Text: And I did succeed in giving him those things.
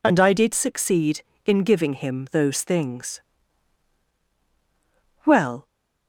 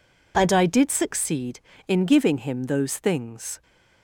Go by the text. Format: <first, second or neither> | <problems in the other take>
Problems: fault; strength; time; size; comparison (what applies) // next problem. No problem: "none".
second | goes on to say "Well"; slight; from 5.2 s on; 0.40 s long